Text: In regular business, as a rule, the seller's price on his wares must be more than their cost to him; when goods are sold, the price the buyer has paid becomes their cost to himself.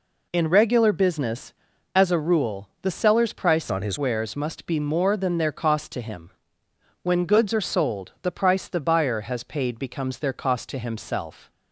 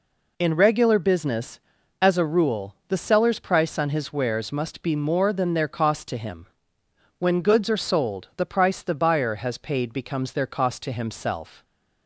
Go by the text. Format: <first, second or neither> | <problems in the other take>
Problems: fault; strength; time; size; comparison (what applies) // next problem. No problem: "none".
second | changes voice from "on" to "his"; from 3.7 to 3.9 s; 0.2 s long